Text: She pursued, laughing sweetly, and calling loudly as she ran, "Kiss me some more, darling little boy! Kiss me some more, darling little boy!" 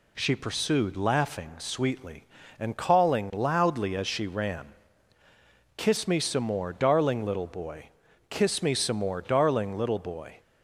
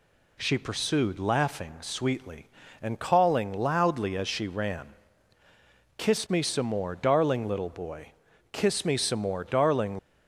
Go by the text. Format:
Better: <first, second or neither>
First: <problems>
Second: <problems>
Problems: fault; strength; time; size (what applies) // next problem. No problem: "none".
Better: first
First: none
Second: stops before "little boy"; at 9.9 s